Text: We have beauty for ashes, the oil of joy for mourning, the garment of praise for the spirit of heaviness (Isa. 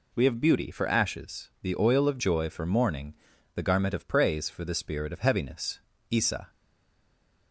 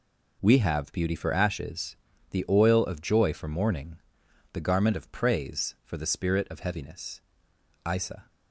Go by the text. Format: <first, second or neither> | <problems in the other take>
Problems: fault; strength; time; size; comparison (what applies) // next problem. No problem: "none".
second | stays silent after the last word; from 6.4 s on; 1.1 s long